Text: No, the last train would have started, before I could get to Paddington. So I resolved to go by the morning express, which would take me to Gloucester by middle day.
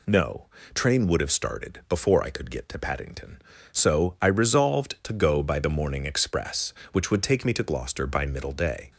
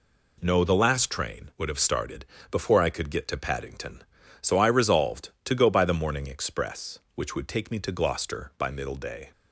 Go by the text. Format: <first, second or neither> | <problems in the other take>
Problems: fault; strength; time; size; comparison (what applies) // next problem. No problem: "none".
second | skips "the last"; at 0.5 s